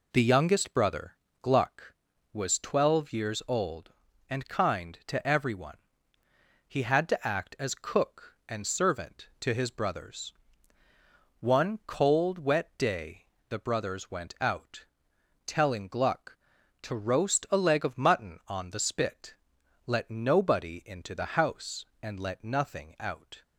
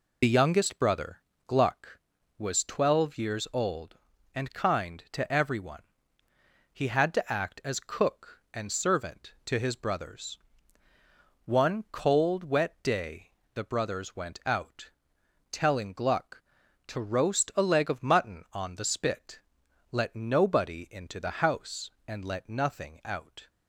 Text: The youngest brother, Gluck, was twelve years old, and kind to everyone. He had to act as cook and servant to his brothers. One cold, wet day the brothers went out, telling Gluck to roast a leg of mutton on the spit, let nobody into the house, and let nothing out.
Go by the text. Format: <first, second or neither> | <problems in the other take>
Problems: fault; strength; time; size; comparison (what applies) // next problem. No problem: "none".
first | loses the start of "The"; at 0.2 s; 45 ms // pauses between "day" and "the"; slight; at 13.2 s; 0.26 s long; slight in the first